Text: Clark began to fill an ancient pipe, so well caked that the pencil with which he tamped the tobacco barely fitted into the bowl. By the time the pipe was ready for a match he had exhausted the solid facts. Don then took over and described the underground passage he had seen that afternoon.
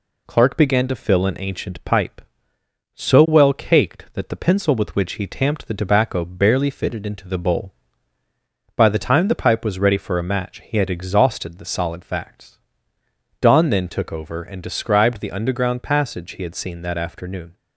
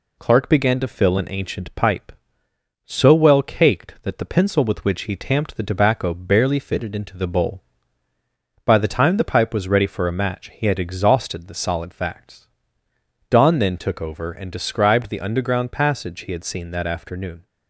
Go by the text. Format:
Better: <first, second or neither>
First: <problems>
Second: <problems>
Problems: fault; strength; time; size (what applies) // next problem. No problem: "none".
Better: neither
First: none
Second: none